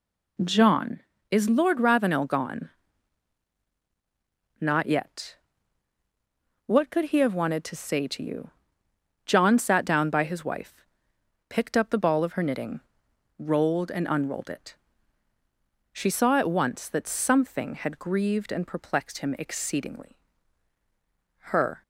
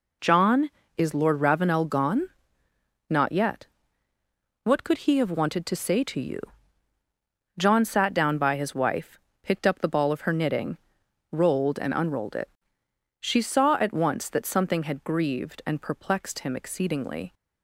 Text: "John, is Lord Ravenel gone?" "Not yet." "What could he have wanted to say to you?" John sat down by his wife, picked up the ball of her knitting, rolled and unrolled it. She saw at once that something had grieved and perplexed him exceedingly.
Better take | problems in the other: second | goes on to say "Her"; slight; from 21.4 s on; 0.32 s long

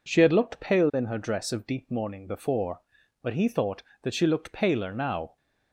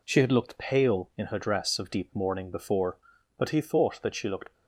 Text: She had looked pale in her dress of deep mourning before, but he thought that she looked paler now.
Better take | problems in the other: first | stops before "paler now"; at 4.5 s

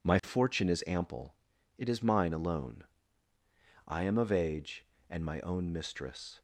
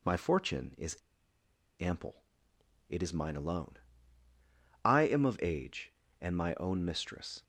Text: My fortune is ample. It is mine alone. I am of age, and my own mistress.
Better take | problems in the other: first | pauses between "is" and "ample"; noticeable; at 0.9 s; 0.82 s long

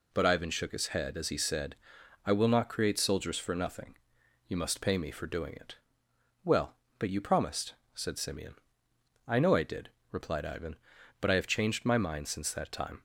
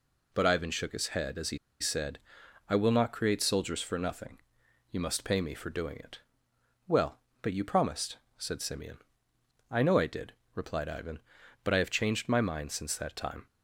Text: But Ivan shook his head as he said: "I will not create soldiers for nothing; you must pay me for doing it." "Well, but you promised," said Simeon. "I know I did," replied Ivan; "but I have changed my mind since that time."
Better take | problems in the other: first | pauses between "he" and "said"; slight; at 1.5 s; 0.22 s long

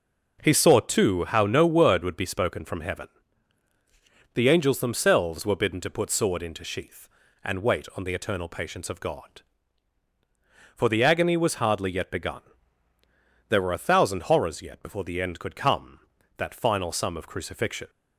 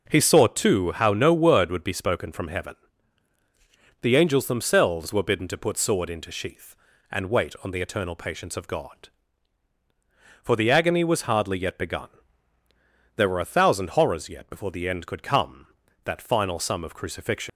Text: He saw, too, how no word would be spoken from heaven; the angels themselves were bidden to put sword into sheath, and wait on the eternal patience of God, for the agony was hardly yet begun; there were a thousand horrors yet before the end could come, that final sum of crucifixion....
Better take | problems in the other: first | leaves "crucifixion" unfinished; at 17.4 s; 70 ms

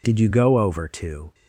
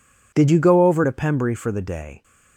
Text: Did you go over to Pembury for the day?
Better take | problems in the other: second | stops before "Pembury for the day"; at 1.3 s

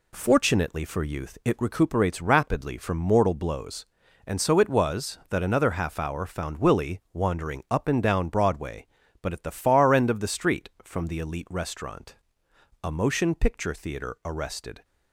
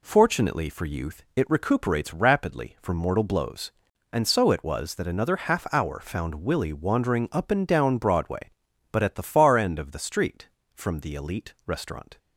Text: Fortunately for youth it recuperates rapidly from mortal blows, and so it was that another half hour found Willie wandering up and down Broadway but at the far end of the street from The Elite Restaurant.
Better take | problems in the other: second | goes on to say "A motion picture theater arrested"; strong; from 12.8 s on; 2.0 s long

